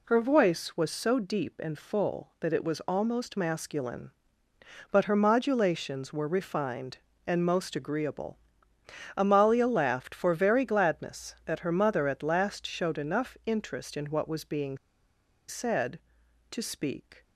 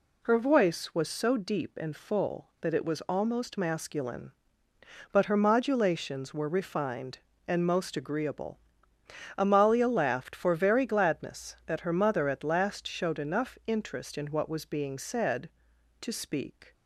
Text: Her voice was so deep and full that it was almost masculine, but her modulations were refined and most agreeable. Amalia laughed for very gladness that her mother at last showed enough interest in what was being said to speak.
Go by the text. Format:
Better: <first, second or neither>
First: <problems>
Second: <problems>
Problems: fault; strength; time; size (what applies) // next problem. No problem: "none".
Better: second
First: pauses between "being" and "said"; noticeable; at 14.7 s; 0.71 s long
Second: none